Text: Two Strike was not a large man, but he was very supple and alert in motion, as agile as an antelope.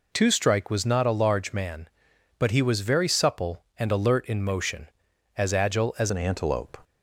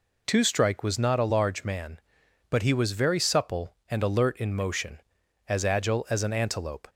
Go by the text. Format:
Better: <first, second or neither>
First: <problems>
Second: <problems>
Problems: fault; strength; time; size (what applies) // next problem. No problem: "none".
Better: second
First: changes voice at "an"; from 6.0 s on; 0.7 s long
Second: none